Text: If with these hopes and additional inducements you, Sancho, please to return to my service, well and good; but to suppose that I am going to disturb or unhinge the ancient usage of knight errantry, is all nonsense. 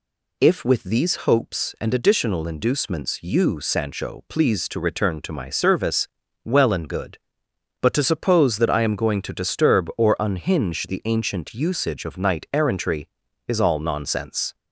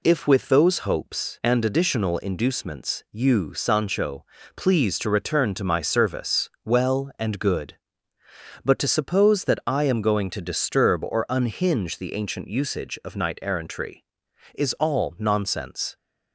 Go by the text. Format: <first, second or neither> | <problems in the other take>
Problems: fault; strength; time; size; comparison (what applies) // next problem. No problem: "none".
first | says "those" for "these"; at 0.4 s